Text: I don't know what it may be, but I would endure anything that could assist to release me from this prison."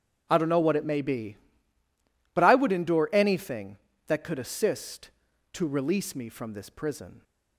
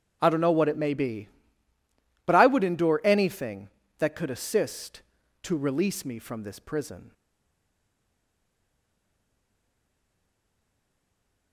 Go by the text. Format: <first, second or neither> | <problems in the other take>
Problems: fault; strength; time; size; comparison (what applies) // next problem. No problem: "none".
first | starts louder than the rest; strong; until 1.2 s; 8 dB; strong in the first // stays silent after the last word; strong; from 7.1 s on; 4.4 s long